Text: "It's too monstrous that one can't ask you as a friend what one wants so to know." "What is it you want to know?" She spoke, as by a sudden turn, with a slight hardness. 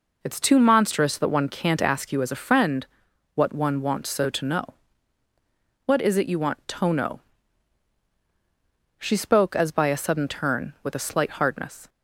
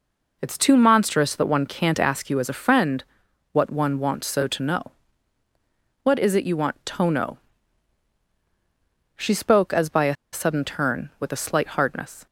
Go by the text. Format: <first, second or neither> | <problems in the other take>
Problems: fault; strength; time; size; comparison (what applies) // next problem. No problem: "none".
first | pauses between "friend" and "what"; noticeable; at 3.0 s; 0.50 s long; noticeable in the first // pauses between "a" and "sudden"; slight; at 10.1 s; 0.18 s long